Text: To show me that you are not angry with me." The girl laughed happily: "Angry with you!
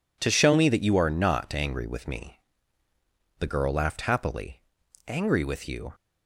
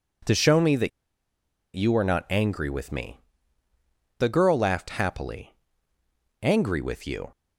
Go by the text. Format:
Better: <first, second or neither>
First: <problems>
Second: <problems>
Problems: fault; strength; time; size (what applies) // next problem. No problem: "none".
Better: first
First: none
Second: pauses between "that" and "you"; noticeable; at 0.8 s; 0.85 s long